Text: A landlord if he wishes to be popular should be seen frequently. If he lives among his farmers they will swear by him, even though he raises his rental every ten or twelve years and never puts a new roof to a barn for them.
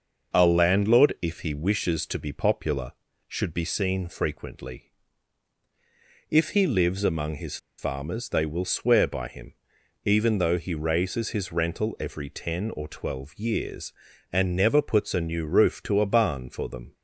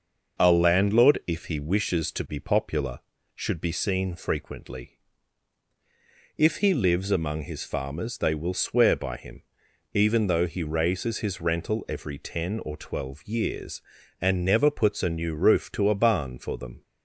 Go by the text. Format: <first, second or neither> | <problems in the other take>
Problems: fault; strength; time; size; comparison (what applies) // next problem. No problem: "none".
second | pauses between "his" and "farmers"; slight; at 7.5 s; 0.20 s long